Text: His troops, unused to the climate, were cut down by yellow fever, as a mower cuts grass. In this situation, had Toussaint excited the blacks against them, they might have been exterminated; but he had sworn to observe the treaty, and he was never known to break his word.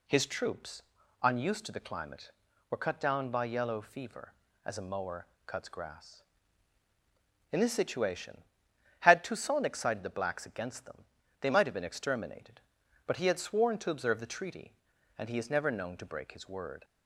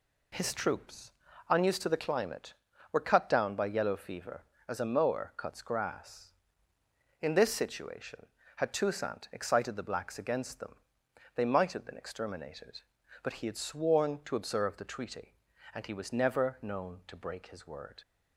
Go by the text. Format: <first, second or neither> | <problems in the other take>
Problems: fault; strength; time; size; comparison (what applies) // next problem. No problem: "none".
second | pauses between "mower" and "cuts"; slight; at 5.2 s; 0.22 s long // says "is" for "was"; at 15.3 s